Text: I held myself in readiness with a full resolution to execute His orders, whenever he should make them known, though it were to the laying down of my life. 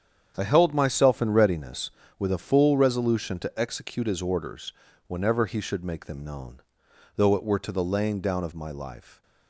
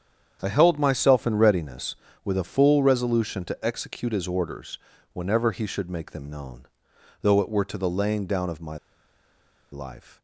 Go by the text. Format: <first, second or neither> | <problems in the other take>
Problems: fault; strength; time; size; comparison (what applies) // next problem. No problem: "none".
first | starts louder than the rest; strong; until 1.4 s; 8.5 dB; strong in the first // pauses between "my" and "life"; noticeable; at 8.7 s; 0.95 s long